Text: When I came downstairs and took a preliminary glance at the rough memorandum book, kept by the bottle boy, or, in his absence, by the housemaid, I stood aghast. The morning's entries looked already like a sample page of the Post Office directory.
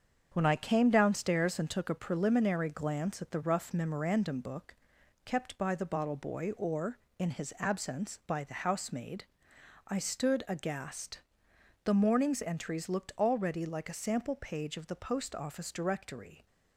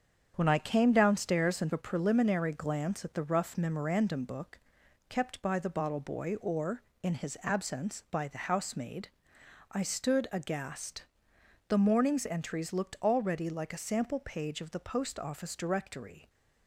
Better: first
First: starts louder than the rest; strong; until 1.3 s; 7 dB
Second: starts louder than the rest; strong; until 1.3 s; 7.5 dB // skips "took"; at 1.7 s

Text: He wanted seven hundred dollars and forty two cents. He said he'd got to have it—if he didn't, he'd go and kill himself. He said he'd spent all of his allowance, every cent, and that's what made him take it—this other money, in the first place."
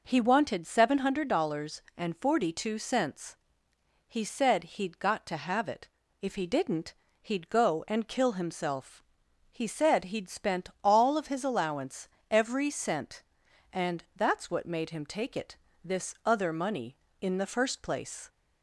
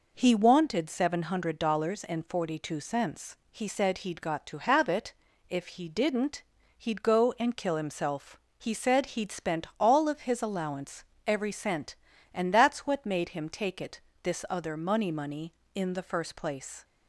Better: first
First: none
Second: says "money" twice; at 15.1 s

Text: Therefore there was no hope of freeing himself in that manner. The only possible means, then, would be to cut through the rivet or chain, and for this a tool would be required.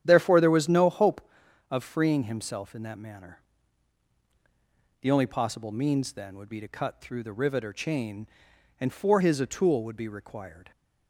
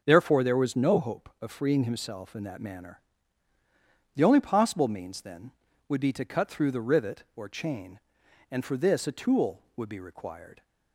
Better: second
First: starts louder than the rest; strong; until 1.0 s; 10 dB // says "his" for "this"; at 9.1 s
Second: starts louder than the rest; until 1.0 s; 6.5 dB

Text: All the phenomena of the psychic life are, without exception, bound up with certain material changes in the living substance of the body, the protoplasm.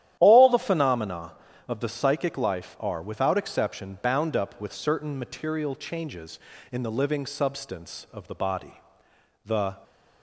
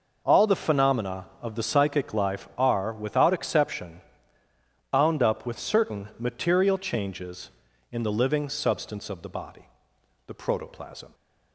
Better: second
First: starts louder than the rest; strong; until 1.1 s; 11.5 dB // stops before "protoplasm"; at 9.8 s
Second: none

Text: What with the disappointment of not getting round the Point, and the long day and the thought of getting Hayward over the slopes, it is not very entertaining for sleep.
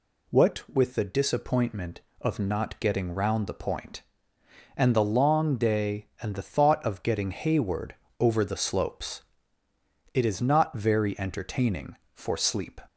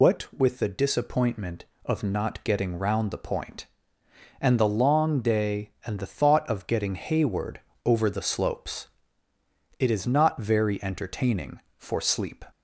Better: first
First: pauses between "Hayward" and "over"; slight; at 7.9 s; 0.26 s long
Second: loses the start of "What"; at 0.0 s; 75 ms // pauses between "Hayward" and "over"; slight; at 7.5 s; 0.26 s long

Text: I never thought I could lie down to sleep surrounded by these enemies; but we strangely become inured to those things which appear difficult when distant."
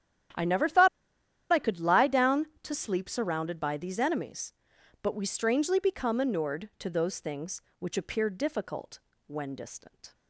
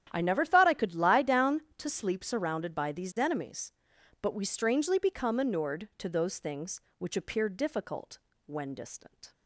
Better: second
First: starts louder than the rest; strong; until 2.0 s; 10.5 dB // pauses between "thought" and "I"; noticeable; at 0.8 s; 0.64 s long // pauses between "difficult" and "when"; slight; at 8.9 s; 0.26 s long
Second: starts louder than the rest; strong; until 1.1 s; 10.5 dB // pauses between "difficult" and "when"; slight; at 8.1 s; 0.26 s long

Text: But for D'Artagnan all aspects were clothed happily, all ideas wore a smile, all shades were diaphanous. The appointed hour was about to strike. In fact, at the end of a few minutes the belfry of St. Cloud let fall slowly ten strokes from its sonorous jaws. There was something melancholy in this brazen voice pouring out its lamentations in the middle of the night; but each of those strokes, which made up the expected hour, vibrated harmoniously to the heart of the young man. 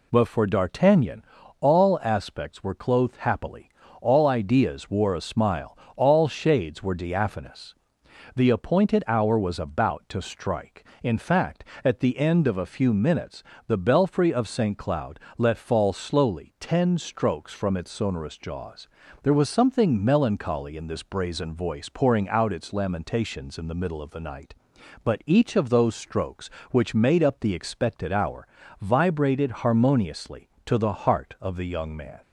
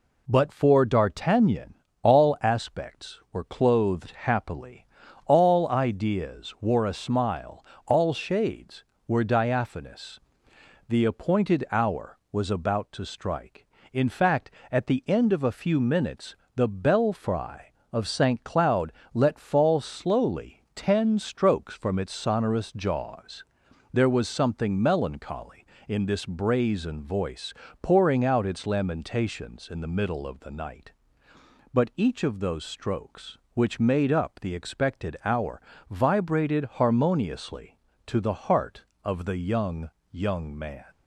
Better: first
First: pauses between "D'Artagnan" and "all"; slight; at 1.2 s; 0.36 s long // pauses between "minutes" and "the"; slight; at 13.4 s; 0.26 s long // pauses between "Cloud" and "let"; slight; at 15.1 s; 0.20 s long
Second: pauses between "D'Artagnan" and "all"; slight; at 1.7 s; 0.28 s long // pauses between "minutes" and "the"; slight; at 16.3 s; 0.20 s long // pauses between "Cloud" and "let"; slight; at 18.9 s; 0.22 s long // pauses between "voice" and "pouring"; slight; at 27.5 s; 0.28 s long // says "young" twice; at 40.1 s

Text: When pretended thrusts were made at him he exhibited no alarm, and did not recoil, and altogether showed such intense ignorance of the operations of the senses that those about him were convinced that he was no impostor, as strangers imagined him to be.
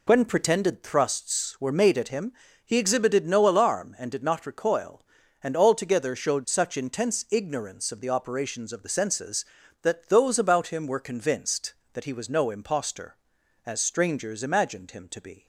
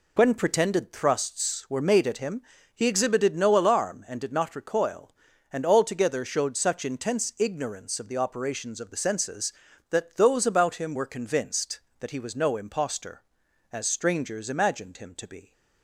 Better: neither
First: pauses between "him" and "he"; slight; at 2.3 s; 0.32 s long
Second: pauses between "him" and "he"; slight; at 2.4 s; 0.32 s long

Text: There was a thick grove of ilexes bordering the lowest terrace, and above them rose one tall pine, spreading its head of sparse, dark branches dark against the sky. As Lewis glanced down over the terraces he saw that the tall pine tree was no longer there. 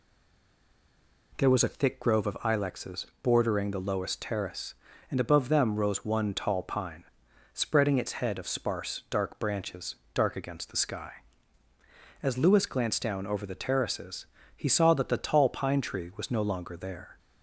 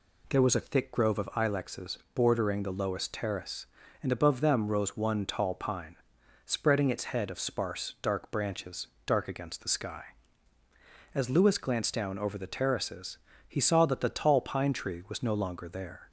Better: second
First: stays silent before the first word; noticeable; until 1.3 s; 1.3 s long // pauses between "ilexes" and "bordering"; slight; at 3.0 s; 0.18 s long // pauses between "branches" and "dark"; slight; at 9.9 s; 0.18 s long // pauses between "terraces" and "he"; slight; at 14.2 s; 0.30 s long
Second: pauses between "ilexes" and "bordering"; slight; at 1.9 s; 0.18 s long // pauses between "branches" and "dark"; slight; at 8.8 s; 0.18 s long // pauses between "terraces" and "he"; slight; at 13.1 s; 0.30 s long

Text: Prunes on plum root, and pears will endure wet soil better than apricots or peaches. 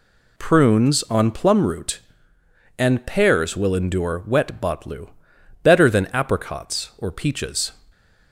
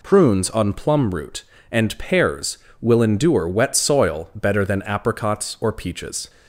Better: second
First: says "botlu" for "soil"; at 4.6 s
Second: none

